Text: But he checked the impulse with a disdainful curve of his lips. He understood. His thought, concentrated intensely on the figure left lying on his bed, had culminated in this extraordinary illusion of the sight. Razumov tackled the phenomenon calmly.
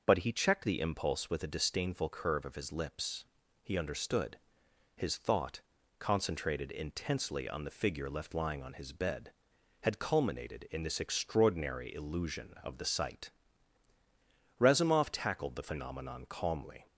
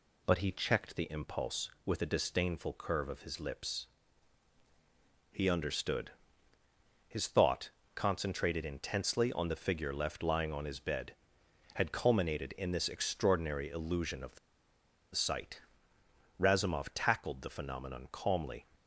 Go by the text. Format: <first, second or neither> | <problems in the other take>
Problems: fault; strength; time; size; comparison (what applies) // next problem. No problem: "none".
first | pauses between "the" and "sight"; noticeable; at 14.3 s; 0.76 s long